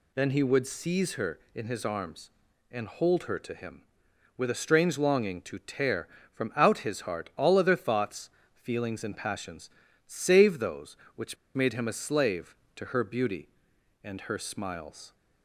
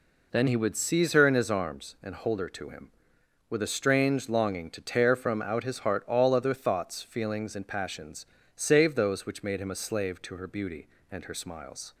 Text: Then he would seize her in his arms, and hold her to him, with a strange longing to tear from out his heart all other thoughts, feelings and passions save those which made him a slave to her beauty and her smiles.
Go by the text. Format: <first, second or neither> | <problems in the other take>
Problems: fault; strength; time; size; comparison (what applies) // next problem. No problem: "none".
second | pauses between "passions" and "save"; slight; at 9.6 s; 0.36 s long; slight in the second // pauses between "which" and "made"; slight; at 11.3 s; 0.19 s long